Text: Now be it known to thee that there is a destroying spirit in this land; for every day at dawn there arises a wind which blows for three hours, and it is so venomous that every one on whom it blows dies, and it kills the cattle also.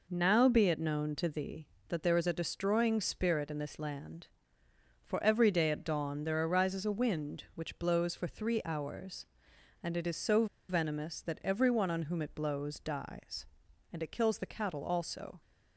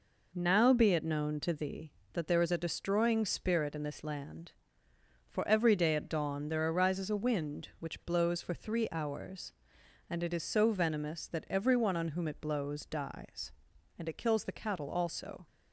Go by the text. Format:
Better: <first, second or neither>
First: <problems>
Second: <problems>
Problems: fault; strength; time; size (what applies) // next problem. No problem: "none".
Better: second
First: pauses between "so" and "venomous"; slight; at 10.4 s; 0.23 s long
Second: none